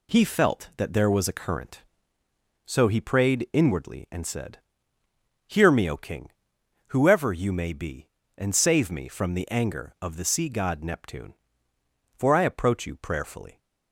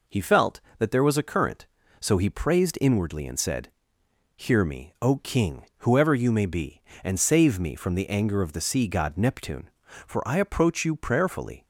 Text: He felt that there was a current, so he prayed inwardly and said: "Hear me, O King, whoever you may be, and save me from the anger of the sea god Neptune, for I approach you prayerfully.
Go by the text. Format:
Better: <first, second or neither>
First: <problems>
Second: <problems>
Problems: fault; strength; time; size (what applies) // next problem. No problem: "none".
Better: first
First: none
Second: says "praised" for "prayed"; at 2.2 s